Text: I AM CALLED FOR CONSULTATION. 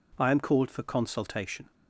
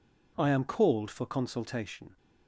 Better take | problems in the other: neither | none

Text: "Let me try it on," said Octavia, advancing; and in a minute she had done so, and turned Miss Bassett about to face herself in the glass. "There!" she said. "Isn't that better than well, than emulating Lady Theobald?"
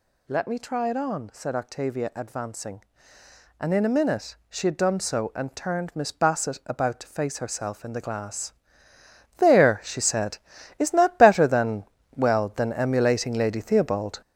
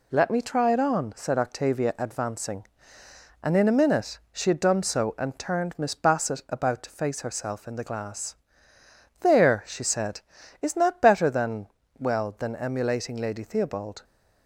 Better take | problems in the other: second | gets louder; strong; throughout; 7.5 dB // pauses between "than" and "well"; slight; at 11.8 s; 0.32 s long; slight in the second

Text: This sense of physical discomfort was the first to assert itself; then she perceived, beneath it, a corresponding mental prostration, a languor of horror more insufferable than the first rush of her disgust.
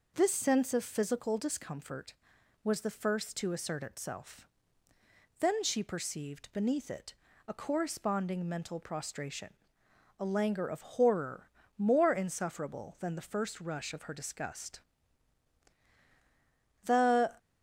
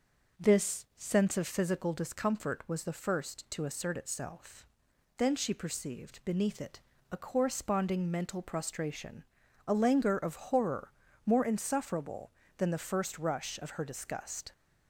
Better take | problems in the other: second | pauses between "horror" and "more"; slight; at 11.4 s; 0.28 s long; slight in the second // goes on to say "The"; from 16.8 s on; 0.50 s long

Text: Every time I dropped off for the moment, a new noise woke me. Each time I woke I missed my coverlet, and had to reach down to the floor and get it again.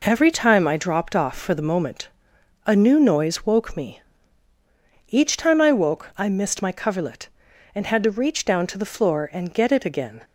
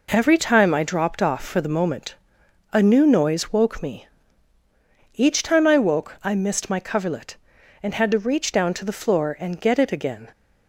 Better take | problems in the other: neither | none

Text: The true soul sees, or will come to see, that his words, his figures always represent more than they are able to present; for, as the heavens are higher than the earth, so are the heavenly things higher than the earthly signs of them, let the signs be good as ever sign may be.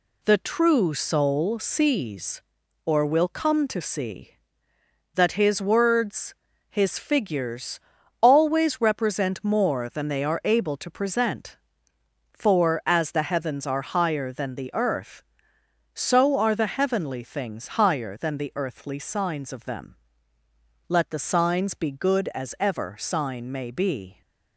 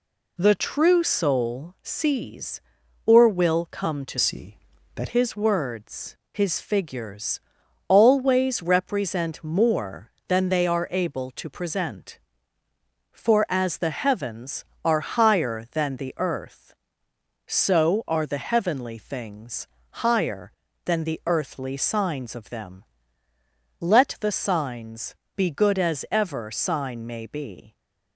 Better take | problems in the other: first | changes voice from "see" to "that"; from 4.1 to 5.0 s; 0.9 s long // pauses between "figures" and "always"; noticeable; at 7.3 s; 0.48 s long; also in the first // pauses between "things" and "higher"; slight; at 19.6 s; 0.34 s long // pauses between "signs" and "be"; slight; at 25.1 s; 0.22 s long

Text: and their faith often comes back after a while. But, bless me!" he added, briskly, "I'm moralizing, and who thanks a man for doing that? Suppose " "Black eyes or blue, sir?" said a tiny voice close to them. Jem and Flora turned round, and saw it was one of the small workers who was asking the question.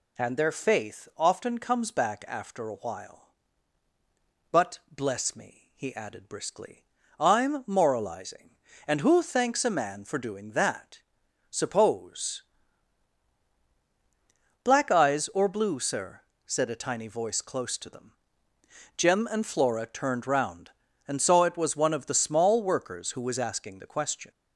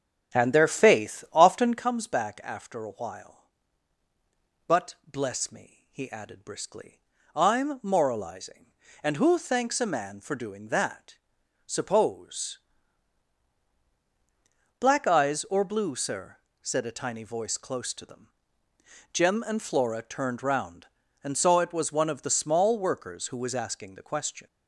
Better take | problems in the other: first | starts louder than the rest; strong; until 1.8 s; 9 dB

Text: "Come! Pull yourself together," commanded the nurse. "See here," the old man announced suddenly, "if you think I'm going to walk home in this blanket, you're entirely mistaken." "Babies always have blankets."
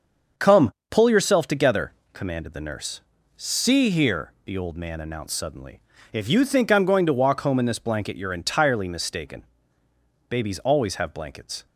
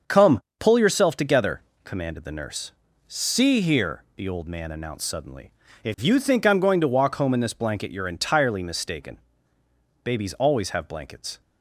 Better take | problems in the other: neither | starts louder than the rest; the same in both

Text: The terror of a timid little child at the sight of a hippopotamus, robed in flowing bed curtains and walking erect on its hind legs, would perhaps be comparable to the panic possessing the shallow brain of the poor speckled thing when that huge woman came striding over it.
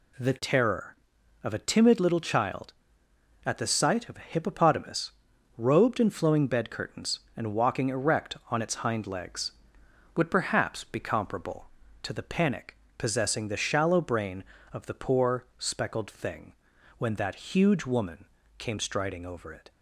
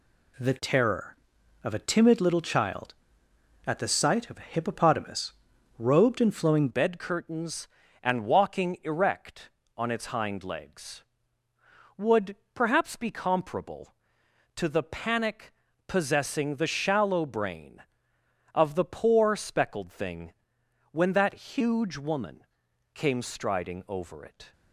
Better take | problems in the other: first | changes voice at "bed"; from 6.7 s on; 17.8 s long // pauses between "would" and "perhaps"; slight; at 12.3 s; 0.18 s long // pauses between "panic" and "possessing"; slight; at 15.5 s; 0.34 s long; slight in the first // pauses between "thing" and "when"; noticeable; at 20.3 s; 0.58 s long; noticeable in the first // pauses between "woman" and "came"; noticeable; at 22.4 s; 0.48 s long; slight in the first

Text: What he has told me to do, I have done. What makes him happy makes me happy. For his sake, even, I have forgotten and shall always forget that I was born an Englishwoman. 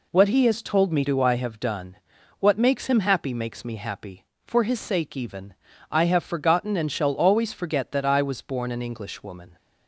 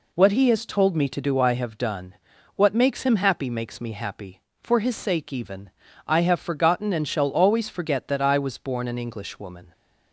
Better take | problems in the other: second | skips "to"; at 1.0 s

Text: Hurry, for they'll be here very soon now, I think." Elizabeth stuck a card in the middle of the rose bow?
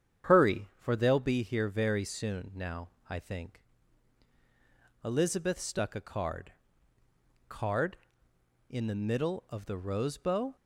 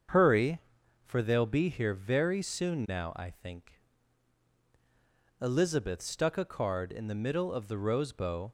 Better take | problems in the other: second | starts louder than the rest; strong; until 1.3 s; 8.5 dB; also in the second // says "card" twice; at 7.4 s

